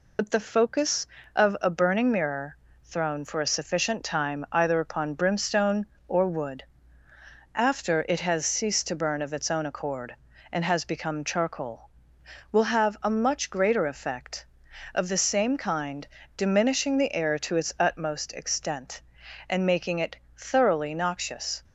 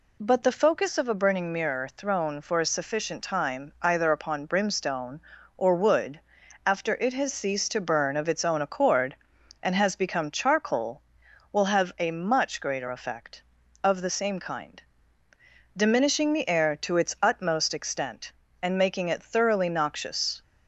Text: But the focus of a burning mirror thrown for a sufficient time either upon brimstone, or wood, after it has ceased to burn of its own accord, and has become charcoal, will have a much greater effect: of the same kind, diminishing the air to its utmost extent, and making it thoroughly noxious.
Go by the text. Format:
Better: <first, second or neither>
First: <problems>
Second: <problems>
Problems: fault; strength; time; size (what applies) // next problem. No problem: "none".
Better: second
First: loses the start of "But"; at 0.1 s; 65 ms // pauses between "mirror" and "thrown"; slight; at 2.5 s; 0.30 s long // pauses between "it" and "thoroughly"; slight; at 20.1 s; 0.18 s long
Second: none